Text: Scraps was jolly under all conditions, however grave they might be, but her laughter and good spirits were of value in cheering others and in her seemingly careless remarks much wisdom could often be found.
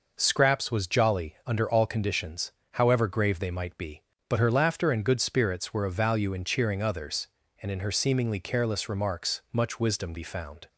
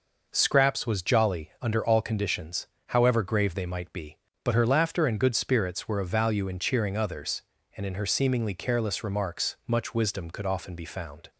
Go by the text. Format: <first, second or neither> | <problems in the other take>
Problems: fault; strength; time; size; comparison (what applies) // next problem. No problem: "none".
second | skips "could often"; at 10.1 s